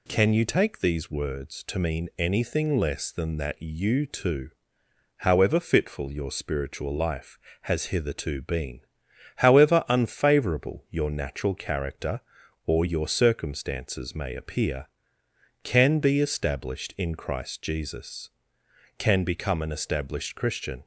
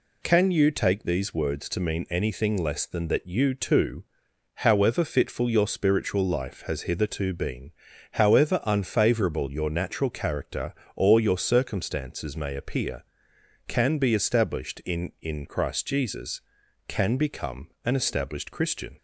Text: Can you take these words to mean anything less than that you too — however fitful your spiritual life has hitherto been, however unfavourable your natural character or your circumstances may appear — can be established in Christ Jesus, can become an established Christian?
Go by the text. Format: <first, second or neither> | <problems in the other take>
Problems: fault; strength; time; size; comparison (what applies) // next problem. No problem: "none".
first | says "in" twice; at 15.2 s // pauses between "become" and "an"; slight; at 17.6 s; 0.16 s long